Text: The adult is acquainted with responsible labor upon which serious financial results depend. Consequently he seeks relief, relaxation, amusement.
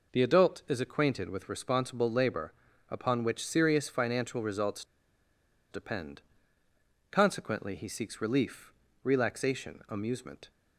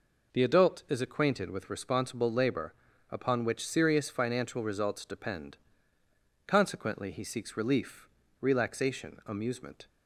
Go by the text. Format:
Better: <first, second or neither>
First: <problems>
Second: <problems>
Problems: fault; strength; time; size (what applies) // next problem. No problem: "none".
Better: second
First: pauses between "labor" and "upon"; slight; at 2.5 s; 0.36 s long // pauses between "results" and "depend"; noticeable; at 4.8 s; 0.87 s long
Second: pauses between "labor" and "upon"; slight; at 2.7 s; 0.36 s long